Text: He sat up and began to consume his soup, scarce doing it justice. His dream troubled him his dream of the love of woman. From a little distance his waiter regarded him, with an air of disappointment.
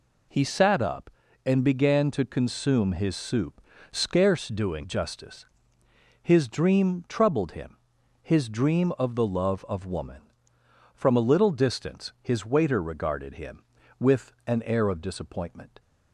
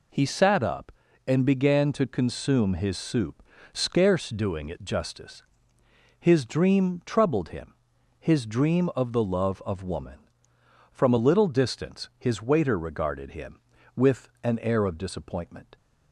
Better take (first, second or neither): second